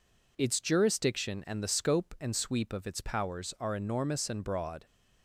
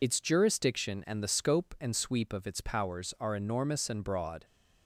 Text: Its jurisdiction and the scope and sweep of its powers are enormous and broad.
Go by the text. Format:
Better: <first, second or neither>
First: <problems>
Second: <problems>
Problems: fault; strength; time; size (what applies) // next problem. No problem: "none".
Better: first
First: none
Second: loses the start of "Its"; at 0.0 s; 50 ms